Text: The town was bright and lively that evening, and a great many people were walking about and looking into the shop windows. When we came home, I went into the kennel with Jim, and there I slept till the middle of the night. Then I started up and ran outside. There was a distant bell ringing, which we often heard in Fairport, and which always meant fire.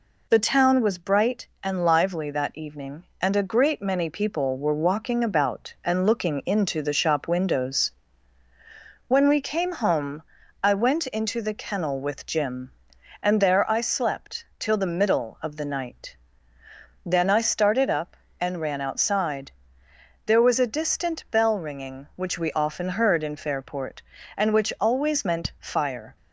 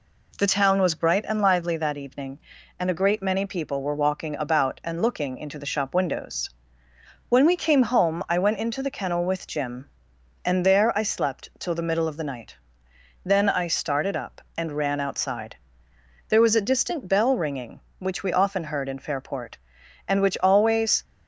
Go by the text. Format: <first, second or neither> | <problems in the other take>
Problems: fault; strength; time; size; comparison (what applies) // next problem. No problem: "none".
first | stops before "meant fire"; at 21.0 s